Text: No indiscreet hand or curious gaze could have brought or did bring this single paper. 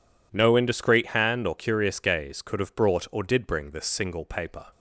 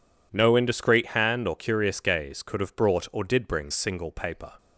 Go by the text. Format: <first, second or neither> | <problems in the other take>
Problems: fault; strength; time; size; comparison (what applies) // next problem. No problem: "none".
first | skips "this"; at 3.7 s